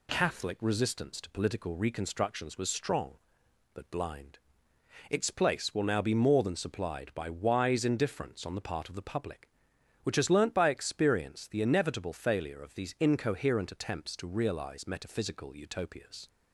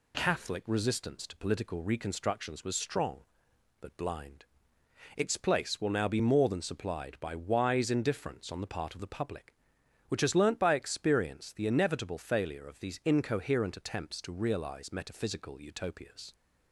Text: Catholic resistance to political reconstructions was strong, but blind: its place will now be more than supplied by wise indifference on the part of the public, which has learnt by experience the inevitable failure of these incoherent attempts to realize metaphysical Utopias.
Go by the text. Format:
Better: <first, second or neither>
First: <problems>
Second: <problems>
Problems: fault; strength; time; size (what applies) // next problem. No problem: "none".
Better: neither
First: none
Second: none